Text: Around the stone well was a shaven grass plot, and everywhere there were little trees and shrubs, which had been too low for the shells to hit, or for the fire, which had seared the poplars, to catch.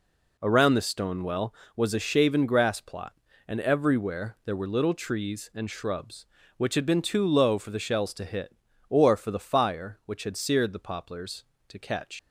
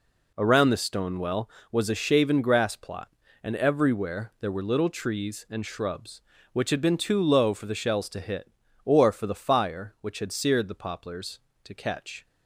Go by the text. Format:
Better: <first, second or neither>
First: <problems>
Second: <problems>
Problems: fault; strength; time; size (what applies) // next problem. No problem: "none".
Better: second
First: leaves "catch" unfinished; at 12.1 s; 100 ms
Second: none